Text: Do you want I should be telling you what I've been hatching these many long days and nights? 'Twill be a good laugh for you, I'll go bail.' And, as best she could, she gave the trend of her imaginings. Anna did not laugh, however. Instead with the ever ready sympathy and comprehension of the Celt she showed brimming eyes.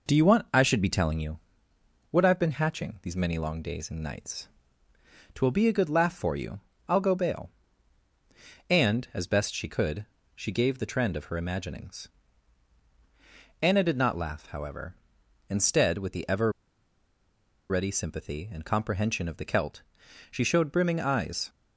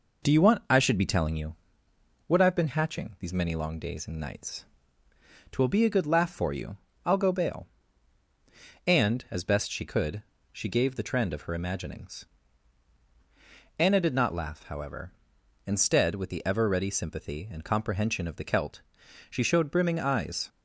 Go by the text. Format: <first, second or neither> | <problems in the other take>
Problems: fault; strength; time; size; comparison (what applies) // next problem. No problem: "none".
second | pauses between "you" and "what"; noticeable; at 1.3 s; 0.74 s long; noticeable in the second // pauses between "ever" and "ready"; at 16.5 s; 1.1 s long // pauses between "Celt" and "she"; noticeable; at 19.8 s; 0.48 s long; noticeable in the second